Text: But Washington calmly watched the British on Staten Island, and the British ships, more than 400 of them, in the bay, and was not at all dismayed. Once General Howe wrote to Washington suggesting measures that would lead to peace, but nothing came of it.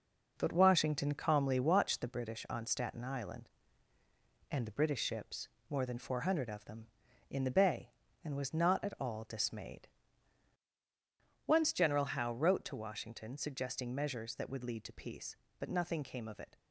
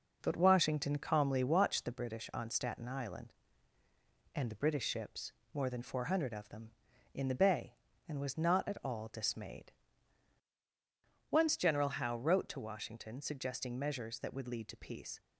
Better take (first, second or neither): first